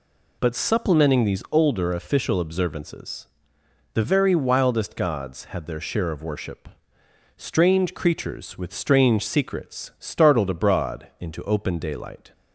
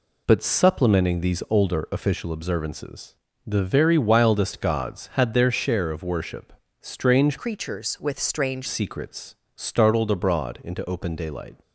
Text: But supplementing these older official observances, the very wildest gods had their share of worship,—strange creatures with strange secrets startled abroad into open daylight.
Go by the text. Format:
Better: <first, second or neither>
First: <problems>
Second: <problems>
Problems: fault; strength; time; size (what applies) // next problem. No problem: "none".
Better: first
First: none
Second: changes voice from "creatures" to "strange"; from 7.3 to 8.6 s; 1.3 s long // pauses between "secrets" and "startled"; slight; at 9.3 s; 0.20 s long